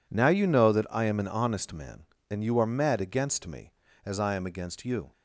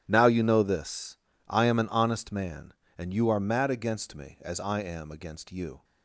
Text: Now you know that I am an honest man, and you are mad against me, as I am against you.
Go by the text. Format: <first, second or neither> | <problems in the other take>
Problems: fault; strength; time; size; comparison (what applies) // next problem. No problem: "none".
first | starts louder than the rest; strong; until 1.0 s; 11.5 dB // says "this" for "that"; at 0.6 s